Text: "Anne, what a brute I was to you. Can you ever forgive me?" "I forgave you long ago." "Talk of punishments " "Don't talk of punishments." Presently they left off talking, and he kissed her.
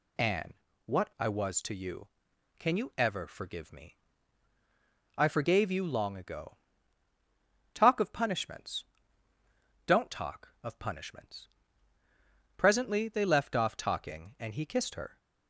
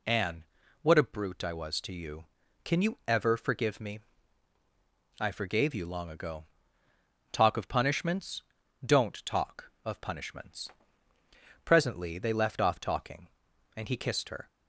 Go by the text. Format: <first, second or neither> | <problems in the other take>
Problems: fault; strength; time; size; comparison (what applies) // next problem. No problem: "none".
second | skips "a brute"; at 1.1 s